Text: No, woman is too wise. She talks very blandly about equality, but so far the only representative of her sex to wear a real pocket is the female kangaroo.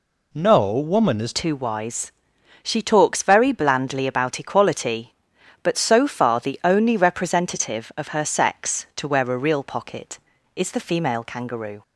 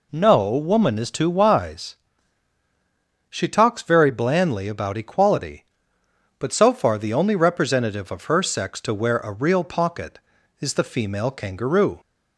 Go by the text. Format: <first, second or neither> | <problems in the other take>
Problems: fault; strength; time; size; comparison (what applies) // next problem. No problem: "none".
second | changes voice at "too"; from 1.3 s on; 10.5 s long